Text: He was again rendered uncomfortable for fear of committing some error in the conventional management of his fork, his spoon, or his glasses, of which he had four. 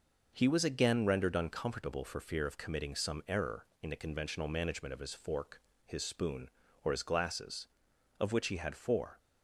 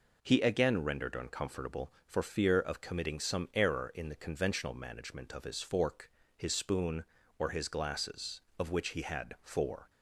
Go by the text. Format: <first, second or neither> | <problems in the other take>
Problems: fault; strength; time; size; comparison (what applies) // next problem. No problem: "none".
first | skips "was"; at 0.4 s